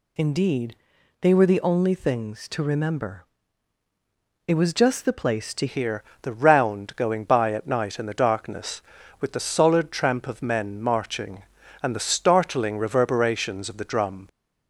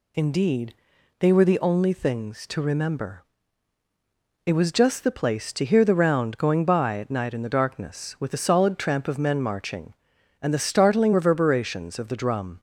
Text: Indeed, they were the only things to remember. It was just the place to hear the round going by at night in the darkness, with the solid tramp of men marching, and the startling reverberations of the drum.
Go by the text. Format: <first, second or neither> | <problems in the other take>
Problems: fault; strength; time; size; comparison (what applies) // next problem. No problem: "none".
second | changes voice at "hear"; from 5.6 s on; 8.6 s long // pauses between "hear" and "the"; slight; at 6.0 s; 0.20 s long